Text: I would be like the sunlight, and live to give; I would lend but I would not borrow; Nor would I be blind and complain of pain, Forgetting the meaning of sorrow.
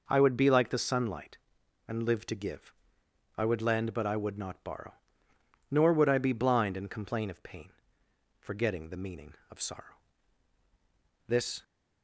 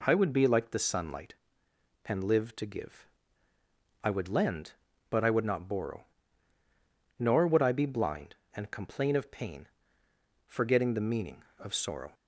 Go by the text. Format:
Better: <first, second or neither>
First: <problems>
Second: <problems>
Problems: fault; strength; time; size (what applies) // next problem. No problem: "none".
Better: second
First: goes on to say "This"; slight; from 11.2 s on; 0.36 s long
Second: none